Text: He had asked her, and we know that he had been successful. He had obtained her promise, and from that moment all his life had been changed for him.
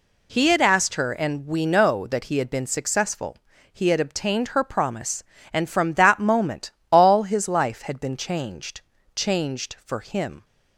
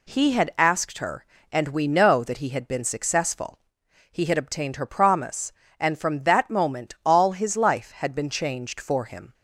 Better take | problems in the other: second | pauses between "moment" and "all"; slight; at 6.7 s; 0.18 s long // says "changed" twice; at 9.1 s

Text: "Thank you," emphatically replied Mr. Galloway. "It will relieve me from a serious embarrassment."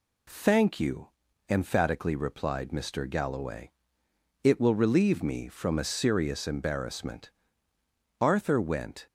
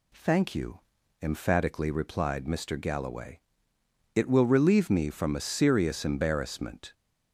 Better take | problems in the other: second | goes on to say "Arthur went"; noticeable; from 8.2 s on; 0.86 s long

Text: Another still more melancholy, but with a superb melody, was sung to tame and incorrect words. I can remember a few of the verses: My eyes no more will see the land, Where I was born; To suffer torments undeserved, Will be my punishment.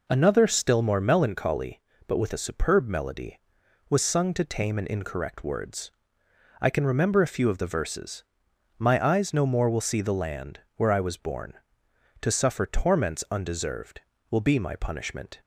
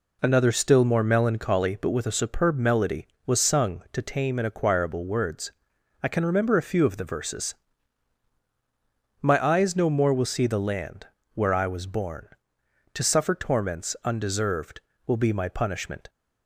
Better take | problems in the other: first | says "acquirable" for "incorrect"; at 4.4 s

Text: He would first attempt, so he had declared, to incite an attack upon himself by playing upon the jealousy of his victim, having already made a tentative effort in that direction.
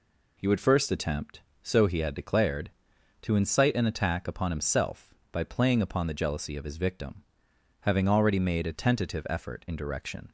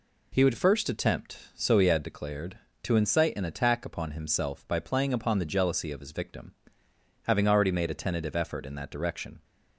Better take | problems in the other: second | skips "that"; at 9.7 s

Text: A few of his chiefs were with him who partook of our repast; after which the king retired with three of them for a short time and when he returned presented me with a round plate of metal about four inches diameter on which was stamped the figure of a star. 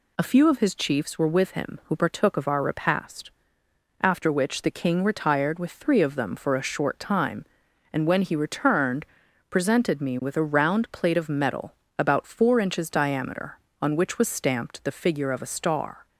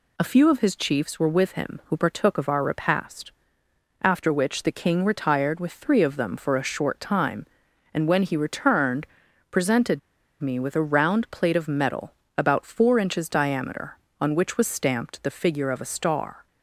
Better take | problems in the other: first | pauses between "returned" and "presented"; noticeable; at 9.0 s; 0.46 s long; noticeable in the first // pauses between "presented" and "me"; at 9.9 s; 0.40 s long // pauses between "metal" and "about"; slight; at 12.1 s; 0.24 s long; slight in the first

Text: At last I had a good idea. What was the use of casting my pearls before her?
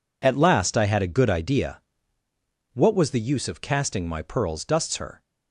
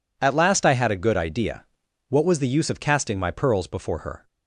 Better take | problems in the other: second | says "dusts" for "before"; at 4.6 s

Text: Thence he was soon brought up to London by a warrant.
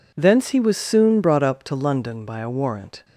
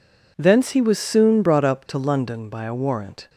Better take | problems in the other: neither | none

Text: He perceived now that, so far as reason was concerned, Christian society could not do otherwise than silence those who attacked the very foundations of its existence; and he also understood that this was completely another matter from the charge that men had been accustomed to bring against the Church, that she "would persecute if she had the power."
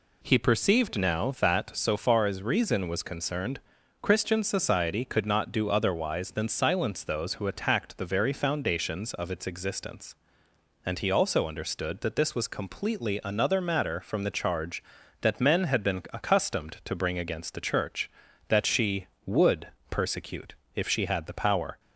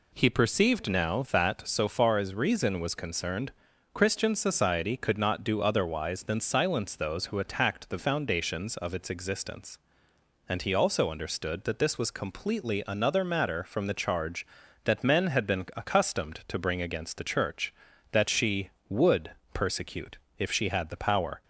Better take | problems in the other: first | skips "very"; at 7.9 s // pauses between "would" and "persecute"; slight; at 19.3 s; 0.20 s long; slight in the first // pauses between "persecute" and "if"; slight; at 20.1 s; 0.22 s long; slight in the first

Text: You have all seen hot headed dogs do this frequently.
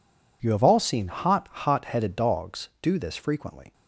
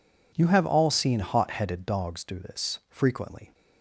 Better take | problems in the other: second | says "hot" twice; at 1.5 s

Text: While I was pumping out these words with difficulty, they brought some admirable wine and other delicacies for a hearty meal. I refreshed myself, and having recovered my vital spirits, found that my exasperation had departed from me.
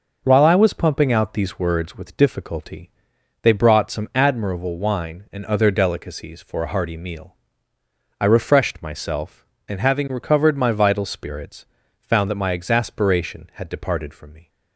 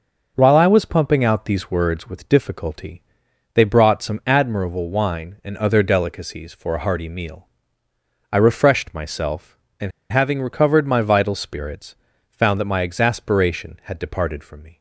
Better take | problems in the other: first | pauses between "and" and "having"; slight; at 9.9 s; 0.21 s long

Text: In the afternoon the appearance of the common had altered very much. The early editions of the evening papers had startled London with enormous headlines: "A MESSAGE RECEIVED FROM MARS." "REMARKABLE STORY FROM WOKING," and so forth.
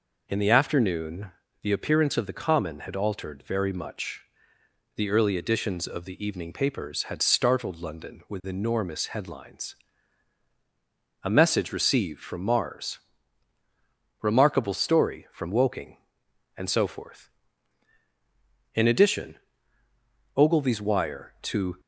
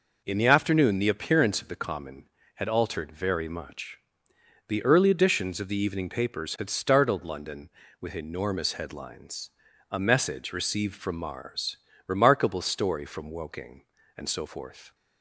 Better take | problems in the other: second | pauses between "afternoon" and "the"; slight; at 1.3 s; 0.32 s long // goes on to say "In addition Ogilvy's wire to"; strong; from 18.7 s on; 3.0 s long

